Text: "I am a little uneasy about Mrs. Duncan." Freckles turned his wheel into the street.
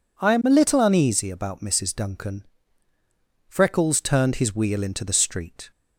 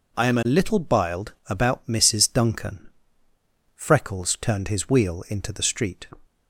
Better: first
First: none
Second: says "biled" for "uneasy"; at 0.7 s

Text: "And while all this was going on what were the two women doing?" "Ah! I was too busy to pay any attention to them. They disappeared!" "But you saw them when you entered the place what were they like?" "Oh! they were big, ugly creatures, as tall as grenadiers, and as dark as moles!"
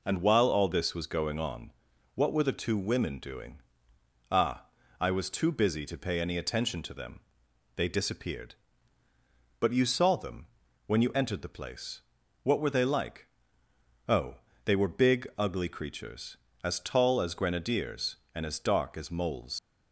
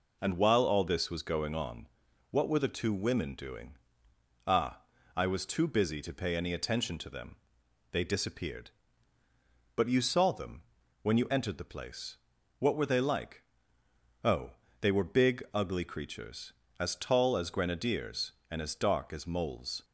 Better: second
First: pauses between "on" and "what"; at 1.7 s; 0.44 s long // pauses between "them" and "when"; at 10.4 s; 0.38 s long // pauses between "place" and "what"; at 12.0 s; 0.42 s long // leaves "moles" unfinished; at 19.5 s; 95 ms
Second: pauses between "on" and "what"; at 1.8 s; 0.44 s long // pauses between "them" and "when"; at 10.6 s; 0.38 s long // pauses between "place" and "what"; at 12.1 s; 0.42 s long

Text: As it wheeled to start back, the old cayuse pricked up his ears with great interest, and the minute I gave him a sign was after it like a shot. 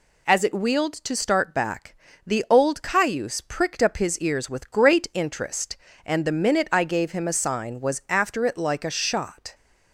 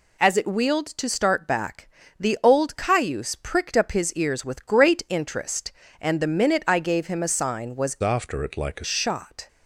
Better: first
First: none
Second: changes voice from "after" to "a"; from 8.0 to 8.8 s; 0.8 s long

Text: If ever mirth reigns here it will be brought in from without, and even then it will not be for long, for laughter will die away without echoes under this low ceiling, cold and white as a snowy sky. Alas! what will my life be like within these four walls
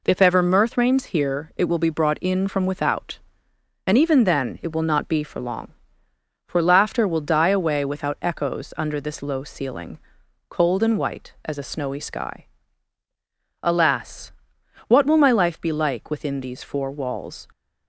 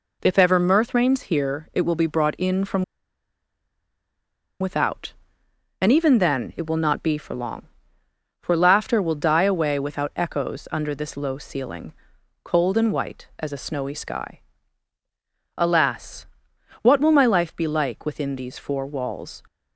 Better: first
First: none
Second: pauses between "from" and "without"; strong; at 2.8 s; 1.7 s long

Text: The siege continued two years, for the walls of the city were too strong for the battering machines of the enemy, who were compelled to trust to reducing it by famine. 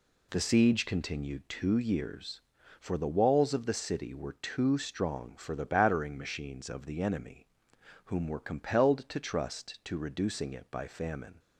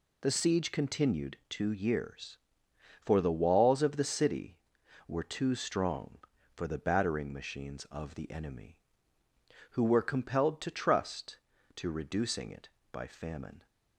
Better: second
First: says "whom" for "who"; at 8.0 s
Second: none

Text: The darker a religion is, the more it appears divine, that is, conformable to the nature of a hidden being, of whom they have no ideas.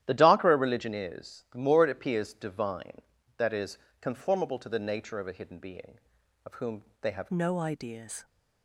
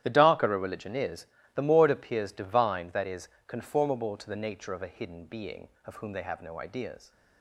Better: second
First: starts louder than the rest; strong; until 1.0 s; 12 dB // pauses between "whom" and "they"; slight; at 6.8 s; 0.20 s long // changes voice at "no"; from 7.3 s on; 0.9 s long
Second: starts louder than the rest; strong; until 1.0 s; 12 dB

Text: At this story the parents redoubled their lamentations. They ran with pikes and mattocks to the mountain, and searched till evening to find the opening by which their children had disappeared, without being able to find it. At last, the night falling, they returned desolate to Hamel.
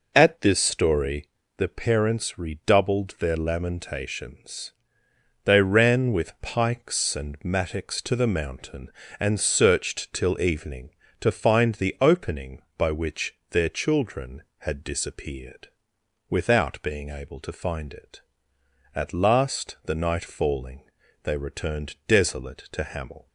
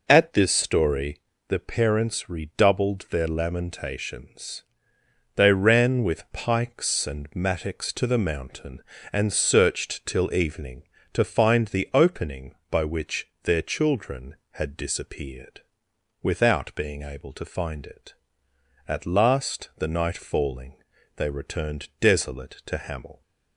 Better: neither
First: pauses between "story" and "the"; slight; at 1.2 s; 0.28 s long // pauses between "which" and "their"; slight; at 13.3 s; 0.16 s long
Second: pauses between "story" and "the"; slight; at 1.2 s; 0.26 s long // pauses between "which" and "their"; slight; at 13.2 s; 0.16 s long

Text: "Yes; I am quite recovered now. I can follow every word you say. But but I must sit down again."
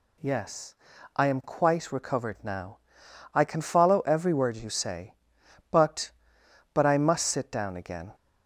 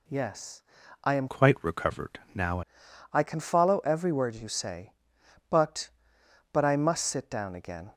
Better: first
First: none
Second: changes voice from "quite" to "now"; from 1.2 to 2.6 s; 1.4 s long

